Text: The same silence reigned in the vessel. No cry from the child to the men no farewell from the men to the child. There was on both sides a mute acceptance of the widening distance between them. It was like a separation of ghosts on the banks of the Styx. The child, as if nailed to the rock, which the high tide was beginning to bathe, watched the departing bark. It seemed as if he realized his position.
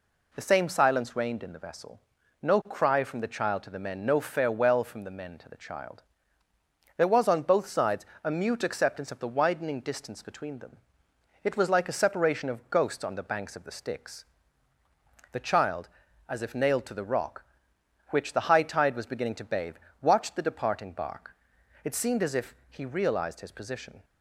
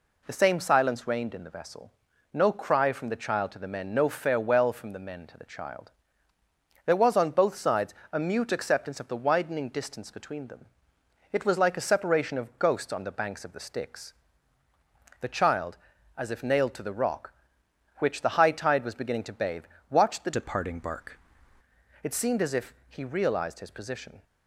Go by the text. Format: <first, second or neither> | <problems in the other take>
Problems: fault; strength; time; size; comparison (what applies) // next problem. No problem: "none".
first | pauses between "sides" and "a"; slight; at 7.9 s; 0.20 s long; slight in the first // changes voice from "departing" to "bark"; from 20.3 to 21.1 s; 0.8 s long